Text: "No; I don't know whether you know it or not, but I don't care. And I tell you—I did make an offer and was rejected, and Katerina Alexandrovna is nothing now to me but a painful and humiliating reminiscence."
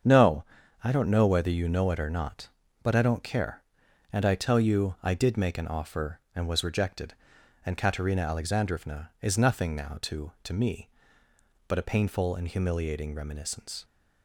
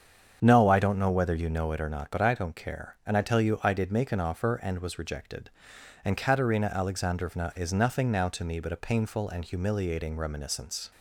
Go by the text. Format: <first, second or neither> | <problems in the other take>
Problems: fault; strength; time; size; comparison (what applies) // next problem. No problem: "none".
second | starts louder than the rest; strong; until 1.4 s; 7.5 dB; strong in the second // says "to" twice; at 10.4 s